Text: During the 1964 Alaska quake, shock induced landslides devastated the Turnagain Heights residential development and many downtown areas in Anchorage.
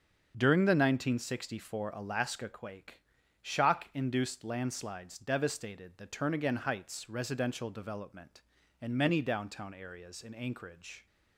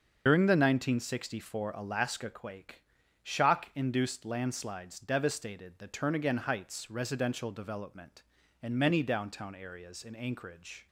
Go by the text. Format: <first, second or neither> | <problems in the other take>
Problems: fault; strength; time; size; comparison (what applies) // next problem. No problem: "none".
first | loses the start of "During"; at 0.2 s; 100 ms // starts louder than the rest; until 1.2 s; 6.5 dB; also in the first